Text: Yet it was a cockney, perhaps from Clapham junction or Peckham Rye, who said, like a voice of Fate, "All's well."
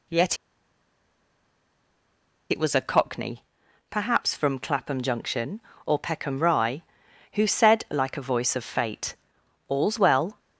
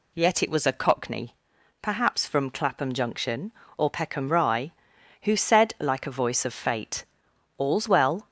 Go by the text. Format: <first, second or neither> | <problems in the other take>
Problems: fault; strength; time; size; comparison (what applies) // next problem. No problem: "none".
second | pauses between "Yet" and "it"; strong; at 0.3 s; 2.1 s long